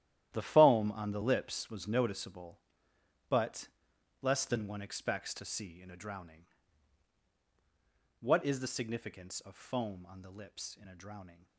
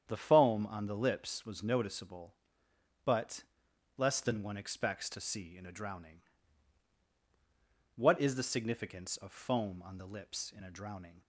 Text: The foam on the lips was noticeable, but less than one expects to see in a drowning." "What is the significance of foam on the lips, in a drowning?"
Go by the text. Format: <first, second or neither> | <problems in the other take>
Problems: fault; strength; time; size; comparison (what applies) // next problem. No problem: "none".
second | gets quieter; strong; throughout; 14 dB // starts louder than the rest; strong; until 1.3 s; 12 dB; strong in the second // pauses between "but" and "less"; noticeable; at 3.6 s; 0.54 s long; noticeable in the second